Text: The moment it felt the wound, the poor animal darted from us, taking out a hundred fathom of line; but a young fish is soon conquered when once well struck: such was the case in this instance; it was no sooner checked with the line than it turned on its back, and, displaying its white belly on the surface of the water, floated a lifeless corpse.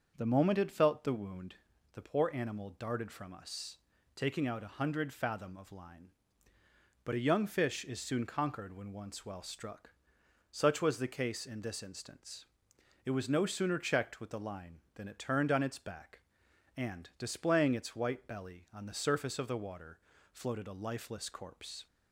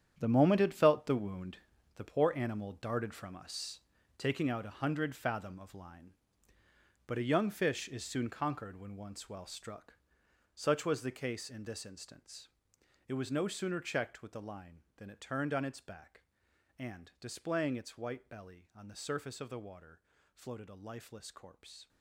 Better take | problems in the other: first | gets quieter; strong; throughout; 12.5 dB // starts louder than the rest; strong; until 1.1 s; 9 dB; also in the first

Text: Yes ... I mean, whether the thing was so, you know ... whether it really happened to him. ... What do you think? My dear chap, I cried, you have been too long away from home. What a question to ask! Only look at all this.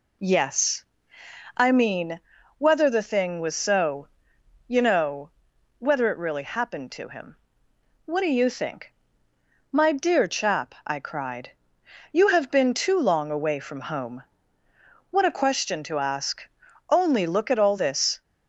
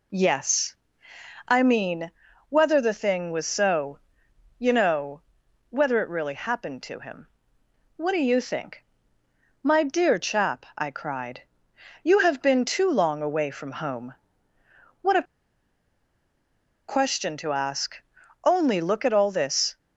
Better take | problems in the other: first | pauses between "a" and "question"; strong; at 15.2 s; 1.6 s long

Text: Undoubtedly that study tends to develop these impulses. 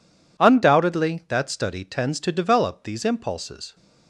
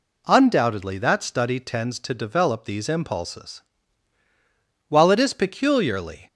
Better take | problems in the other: first | goes on to say "While it is peculiarly"; from 4.8 s on; 1.3 s long

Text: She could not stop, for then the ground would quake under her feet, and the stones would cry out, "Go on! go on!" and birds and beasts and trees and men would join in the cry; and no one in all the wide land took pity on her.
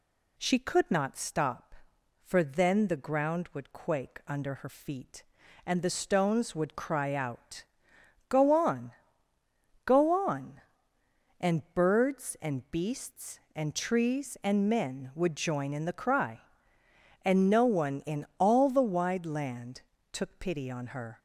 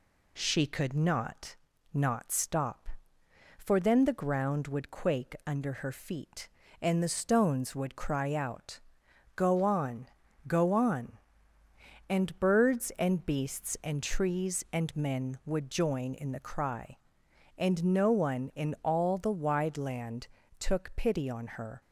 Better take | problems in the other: first | says "not" twice; at 1.9 s // pauses between "land" and "took"; slight; at 20.2 s; 0.32 s long; slight in the first

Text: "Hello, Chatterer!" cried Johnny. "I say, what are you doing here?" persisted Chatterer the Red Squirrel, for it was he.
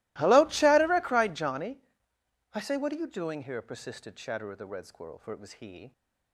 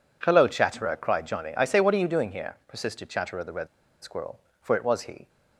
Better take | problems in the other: first | pauses between "Red" and "Squirrel"; at 3.6 s; 0.36 s long

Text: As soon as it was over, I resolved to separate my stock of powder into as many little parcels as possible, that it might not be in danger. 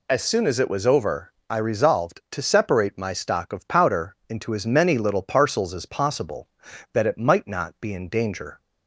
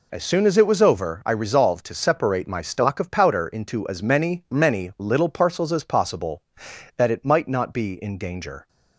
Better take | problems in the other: first | says "many" twice; at 4.5 s

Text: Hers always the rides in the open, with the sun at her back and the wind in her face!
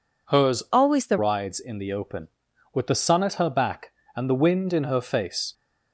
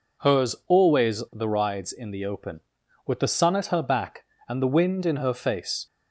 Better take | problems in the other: second | changes voice from "always" to "the"; from 0.7 to 1.1 s; 0.4 s long

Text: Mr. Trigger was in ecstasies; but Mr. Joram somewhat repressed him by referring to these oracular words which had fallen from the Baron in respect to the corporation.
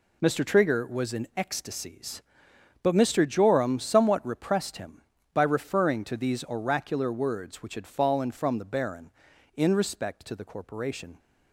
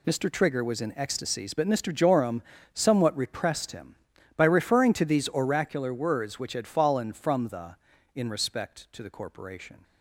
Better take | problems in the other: first | pauses between "Joram" and "somewhat"; slight; at 2.4 s; 0.30 s long // skips "Baron"; at 7.9 s

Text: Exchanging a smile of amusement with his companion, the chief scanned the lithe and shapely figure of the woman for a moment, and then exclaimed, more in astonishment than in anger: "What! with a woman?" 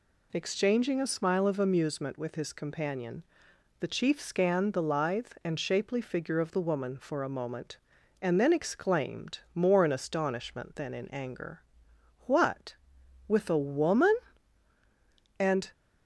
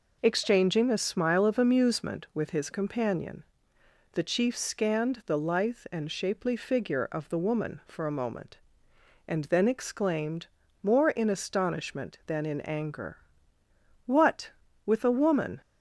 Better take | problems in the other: second | goes on to say "And"; slight; from 15.4 s on; 0.32 s long

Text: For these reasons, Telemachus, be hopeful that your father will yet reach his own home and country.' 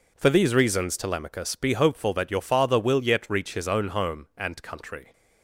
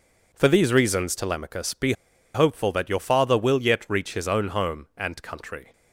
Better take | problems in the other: first | pauses between "be" and "hopeful"; at 1.9 s; 0.41 s long

